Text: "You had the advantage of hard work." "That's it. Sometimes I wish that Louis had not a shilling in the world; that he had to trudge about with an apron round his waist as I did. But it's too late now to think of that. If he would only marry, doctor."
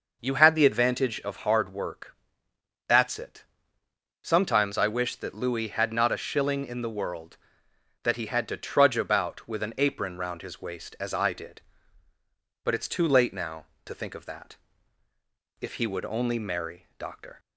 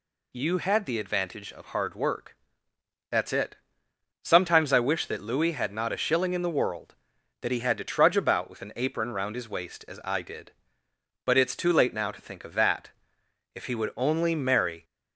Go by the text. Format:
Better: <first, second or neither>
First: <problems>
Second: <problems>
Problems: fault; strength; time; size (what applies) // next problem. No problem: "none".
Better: first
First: none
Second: stops before "doctor"; at 14.8 s